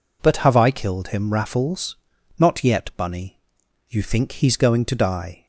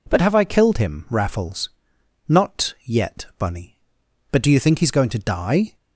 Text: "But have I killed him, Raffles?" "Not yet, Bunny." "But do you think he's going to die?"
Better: second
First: skips "But do"; at 3.6 s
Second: none

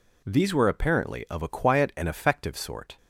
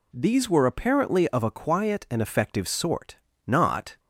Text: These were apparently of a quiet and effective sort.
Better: first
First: none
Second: goes on to say "Not"; from 3.4 s on; 0.54 s long

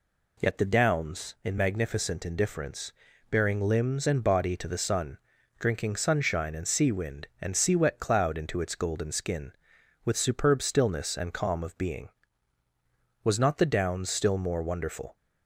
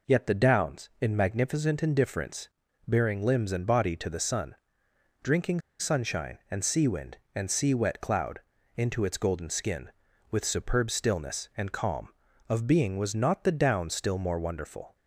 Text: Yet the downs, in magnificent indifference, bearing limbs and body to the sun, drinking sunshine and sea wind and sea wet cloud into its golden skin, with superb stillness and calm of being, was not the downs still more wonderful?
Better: first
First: none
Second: pauses between "drinking" and "sunshine"; slight; at 5.6 s; 0.19 s long // pauses between "cloud" and "into"; at 8.3 s; 0.38 s long

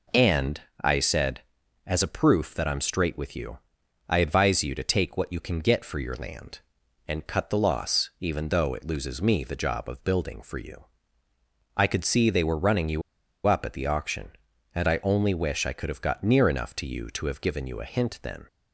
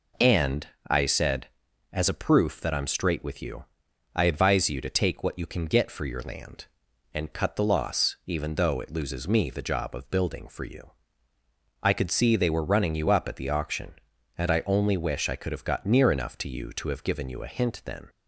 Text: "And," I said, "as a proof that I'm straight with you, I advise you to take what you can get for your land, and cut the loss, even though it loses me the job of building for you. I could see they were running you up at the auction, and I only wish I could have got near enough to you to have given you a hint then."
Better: second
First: pauses between "you" and "up"; at 13.0 s; 0.45 s long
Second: none

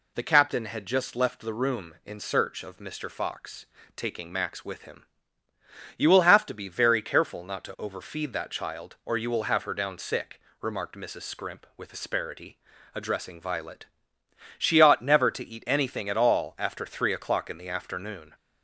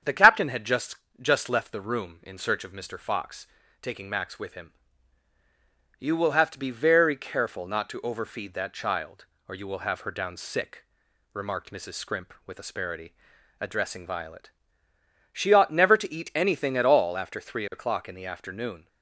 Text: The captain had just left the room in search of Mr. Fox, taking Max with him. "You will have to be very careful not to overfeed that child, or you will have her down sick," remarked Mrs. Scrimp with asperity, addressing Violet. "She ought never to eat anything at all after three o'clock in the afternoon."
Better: first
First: none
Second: starts louder than the rest; strong; until 1.3 s; 8 dB // says "just" twice; at 1.2 s

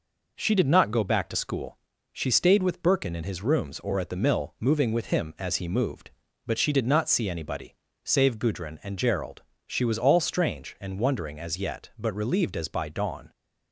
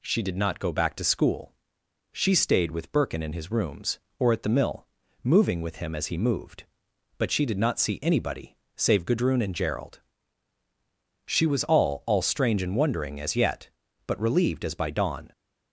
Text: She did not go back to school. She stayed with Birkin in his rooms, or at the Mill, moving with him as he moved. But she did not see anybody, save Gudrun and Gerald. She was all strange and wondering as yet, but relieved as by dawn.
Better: first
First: none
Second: says "all" twice; at 12.0 s

